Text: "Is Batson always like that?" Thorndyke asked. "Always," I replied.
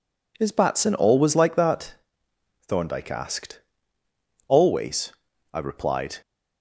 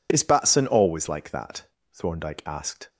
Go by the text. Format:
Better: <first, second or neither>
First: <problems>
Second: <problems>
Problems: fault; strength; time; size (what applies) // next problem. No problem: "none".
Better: first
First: none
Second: stops before "Always I replied"; at 2.8 s